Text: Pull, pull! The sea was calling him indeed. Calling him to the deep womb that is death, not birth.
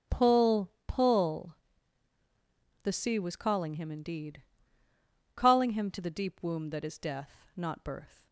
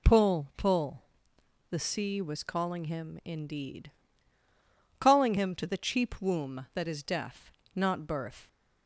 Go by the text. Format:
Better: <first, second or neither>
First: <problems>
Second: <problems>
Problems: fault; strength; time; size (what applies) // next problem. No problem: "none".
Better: first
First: none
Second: says "cheap" for "deep"; at 5.7 s